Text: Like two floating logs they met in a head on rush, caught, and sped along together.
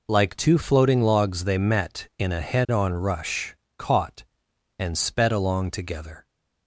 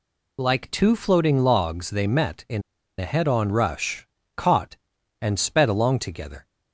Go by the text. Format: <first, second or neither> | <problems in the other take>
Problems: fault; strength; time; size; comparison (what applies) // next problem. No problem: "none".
first | pauses between "in" and "a"; at 2.6 s; 0.38 s long